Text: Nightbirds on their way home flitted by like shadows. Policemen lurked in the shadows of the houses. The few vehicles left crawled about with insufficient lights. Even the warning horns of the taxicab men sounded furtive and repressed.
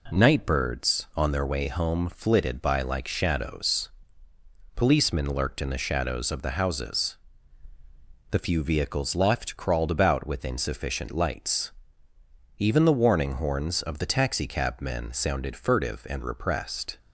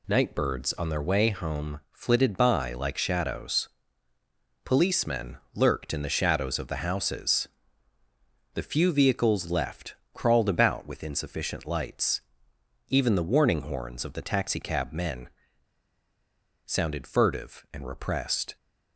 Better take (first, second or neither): first